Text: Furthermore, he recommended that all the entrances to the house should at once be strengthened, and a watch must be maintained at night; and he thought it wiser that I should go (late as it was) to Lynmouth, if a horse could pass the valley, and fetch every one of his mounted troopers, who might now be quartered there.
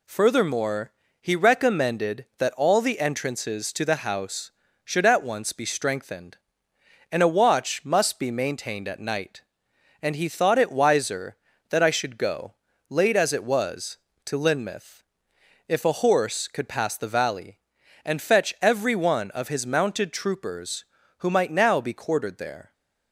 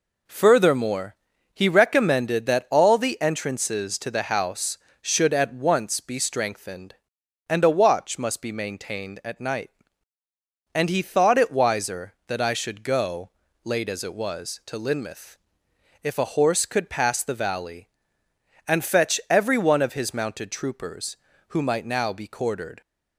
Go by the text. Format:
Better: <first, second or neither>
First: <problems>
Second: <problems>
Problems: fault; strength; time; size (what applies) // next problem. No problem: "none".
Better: first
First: none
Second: stops before "there"; at 22.8 s